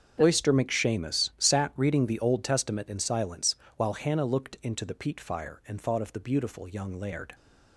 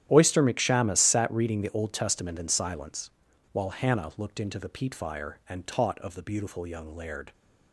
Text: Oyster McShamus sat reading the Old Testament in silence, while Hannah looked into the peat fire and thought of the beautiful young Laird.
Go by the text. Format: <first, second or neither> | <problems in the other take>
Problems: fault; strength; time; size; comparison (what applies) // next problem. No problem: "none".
first | starts louder than the rest; strong; until 1.1 s; 11 dB; strong in the first // says "taught" for "thought"; at 5.6 s